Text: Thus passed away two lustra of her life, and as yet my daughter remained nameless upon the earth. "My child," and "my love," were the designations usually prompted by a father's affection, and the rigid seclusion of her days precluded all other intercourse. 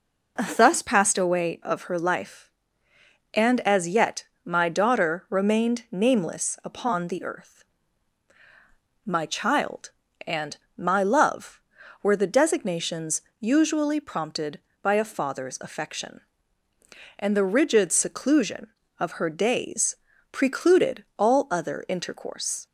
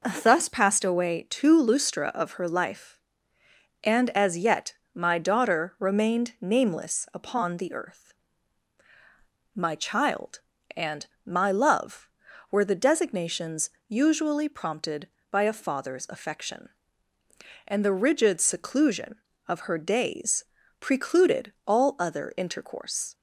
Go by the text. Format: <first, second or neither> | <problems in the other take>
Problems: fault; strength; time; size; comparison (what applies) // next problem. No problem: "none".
second | skips "two lustra"; at 1.6 s // pauses between "yet" and "my"; slight; at 4.2 s; 0.20 s long; slight in the second // pauses between "and" and "my"; slight; at 10.5 s; 0.18 s long; slight in the second // pauses between "designations" and "usually"; slight; at 13.2 s; 0.18 s long; slight in the second // pauses between "days" and "precluded"; at 19.9 s; 0.38 s long; also in the second